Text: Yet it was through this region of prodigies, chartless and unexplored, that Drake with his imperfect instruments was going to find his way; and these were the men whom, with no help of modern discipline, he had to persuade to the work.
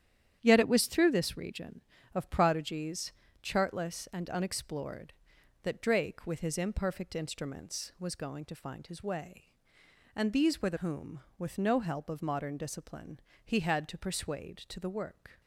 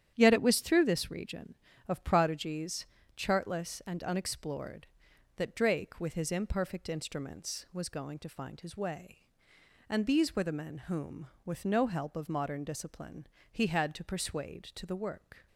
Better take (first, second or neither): second